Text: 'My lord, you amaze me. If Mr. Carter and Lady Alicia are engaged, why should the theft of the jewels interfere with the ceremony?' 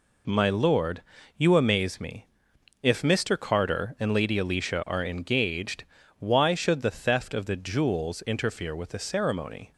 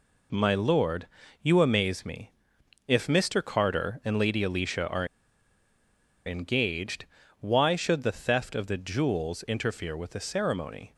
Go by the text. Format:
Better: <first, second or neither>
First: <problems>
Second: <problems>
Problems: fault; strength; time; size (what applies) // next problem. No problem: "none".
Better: first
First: none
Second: pauses between "are" and "engaged"; at 5.0 s; 1.2 s long